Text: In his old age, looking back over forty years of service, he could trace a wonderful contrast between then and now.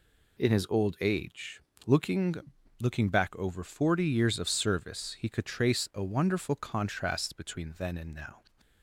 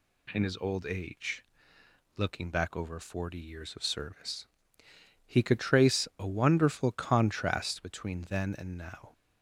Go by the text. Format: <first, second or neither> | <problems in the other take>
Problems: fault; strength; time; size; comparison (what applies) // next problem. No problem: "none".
second | says "looking" twice; at 2.7 s